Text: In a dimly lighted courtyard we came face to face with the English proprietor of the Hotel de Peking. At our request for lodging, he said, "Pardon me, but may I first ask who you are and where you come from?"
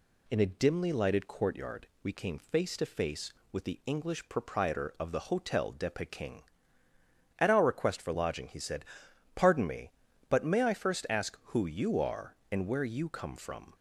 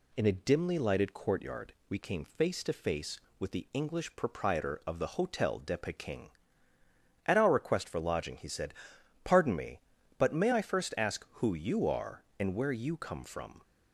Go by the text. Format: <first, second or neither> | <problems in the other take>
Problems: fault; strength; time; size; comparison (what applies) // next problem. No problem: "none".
neither | none